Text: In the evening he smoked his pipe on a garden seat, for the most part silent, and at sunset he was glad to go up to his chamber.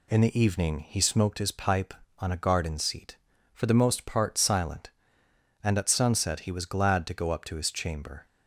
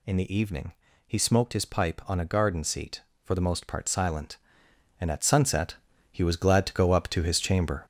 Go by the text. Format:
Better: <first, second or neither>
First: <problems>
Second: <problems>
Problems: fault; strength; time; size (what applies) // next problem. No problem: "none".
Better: first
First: none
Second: gets louder; throughout; 7 dB // pauses between "evening" and "he"; slight; at 0.7 s; 0.34 s long // pauses between "sunset" and "he"; slight; at 5.7 s; 0.36 s long